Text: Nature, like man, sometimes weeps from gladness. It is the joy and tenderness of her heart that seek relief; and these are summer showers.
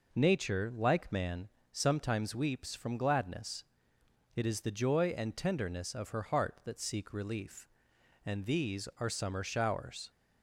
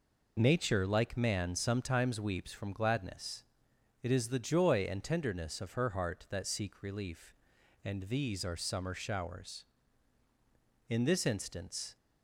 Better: first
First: none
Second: goes on to say "In this instance"; noticeable; from 10.8 s on; 1.0 s long

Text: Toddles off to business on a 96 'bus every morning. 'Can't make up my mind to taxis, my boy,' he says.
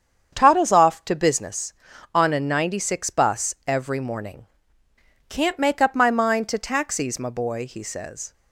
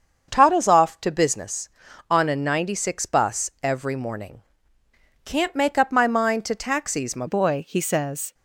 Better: first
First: starts louder than the rest; strong; until 1.3 s; 7.5 dB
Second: starts louder than the rest; until 1.3 s; 7 dB // changes voice at "boy"; from 7.2 s on; 1.1 s long

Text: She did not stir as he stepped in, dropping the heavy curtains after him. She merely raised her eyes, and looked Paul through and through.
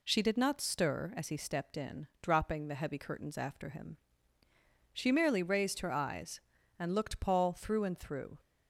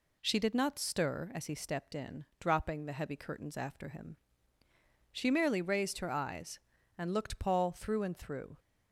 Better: neither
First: none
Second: none

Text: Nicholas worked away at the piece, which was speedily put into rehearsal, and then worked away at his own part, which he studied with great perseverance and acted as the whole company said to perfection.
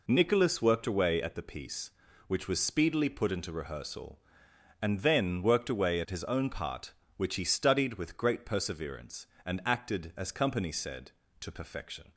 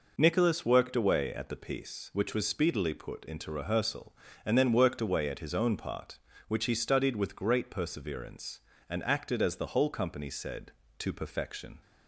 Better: second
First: skips "the whole"; at 10.3 s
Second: none

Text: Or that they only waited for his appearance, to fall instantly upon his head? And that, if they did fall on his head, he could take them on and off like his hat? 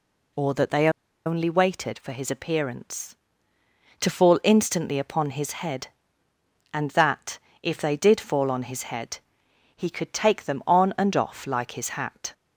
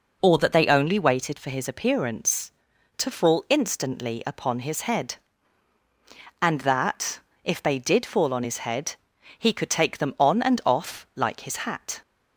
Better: second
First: pauses between "they" and "only"; at 0.8 s; 0.38 s long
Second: none

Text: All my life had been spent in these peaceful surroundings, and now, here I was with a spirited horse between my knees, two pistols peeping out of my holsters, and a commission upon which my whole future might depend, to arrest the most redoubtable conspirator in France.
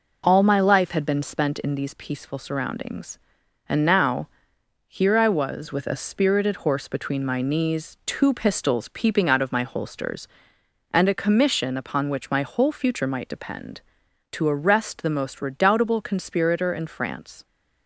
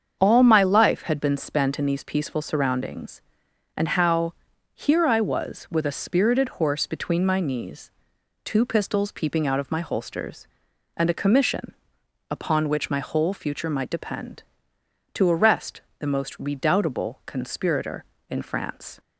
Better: first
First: none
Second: starts louder than the rest; strong; until 1.2 s; 7 dB // says "how" for "now"; at 3.8 s // pauses between "commission" and "upon"; noticeable; at 11.7 s; 0.56 s long // pauses between "arrest" and "the"; slight; at 15.8 s; 0.18 s long

